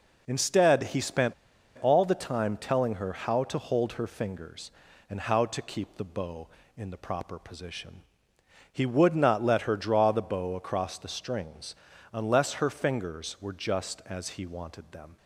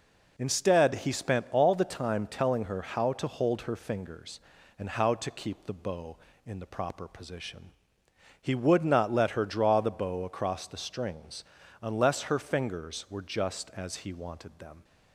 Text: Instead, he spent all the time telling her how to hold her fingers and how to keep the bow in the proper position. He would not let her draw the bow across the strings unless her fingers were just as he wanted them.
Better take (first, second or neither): second